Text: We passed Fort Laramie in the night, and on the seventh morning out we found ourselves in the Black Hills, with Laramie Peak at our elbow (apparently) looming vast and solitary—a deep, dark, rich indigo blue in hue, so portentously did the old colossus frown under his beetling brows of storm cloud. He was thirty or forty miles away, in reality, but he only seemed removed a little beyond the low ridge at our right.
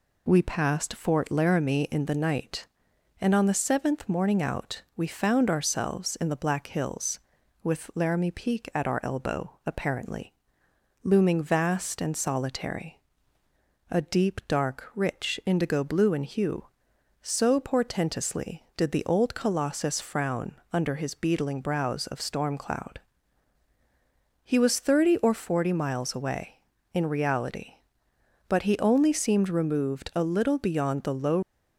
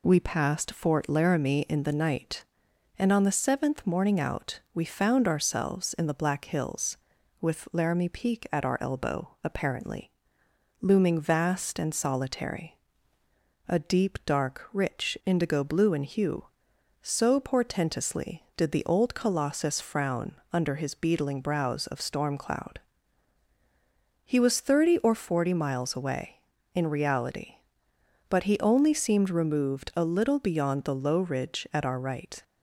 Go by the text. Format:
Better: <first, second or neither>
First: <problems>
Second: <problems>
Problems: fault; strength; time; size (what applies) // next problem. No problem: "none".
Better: second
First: pauses between "out" and "we"; slight; at 4.8 s; 0.16 s long // pauses between "frown" and "under"; slight; at 20.5 s; 0.18 s long // stops before "ridge at our right"; at 31.4 s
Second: pauses between "out" and "we"; slight; at 4.5 s; 0.16 s long // pauses between "frown" and "under"; slight; at 20.3 s; 0.18 s long